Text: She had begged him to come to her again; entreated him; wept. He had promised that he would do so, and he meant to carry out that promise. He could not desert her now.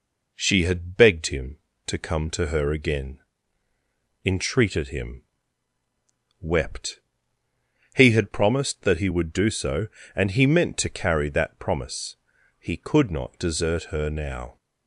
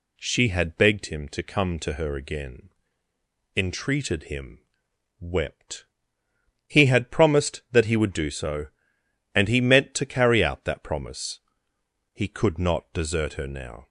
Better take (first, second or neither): second